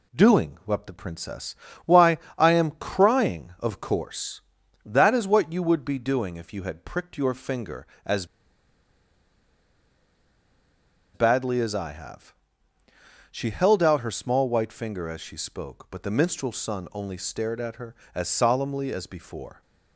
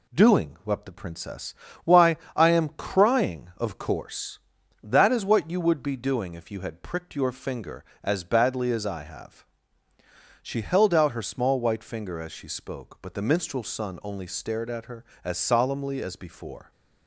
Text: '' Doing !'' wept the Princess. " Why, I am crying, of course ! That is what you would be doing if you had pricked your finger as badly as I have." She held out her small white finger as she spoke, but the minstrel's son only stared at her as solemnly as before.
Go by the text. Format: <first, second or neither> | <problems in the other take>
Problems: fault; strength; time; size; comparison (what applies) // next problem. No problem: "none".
second | pauses between "as" and "badly"; strong; at 8.2 s; 2.8 s long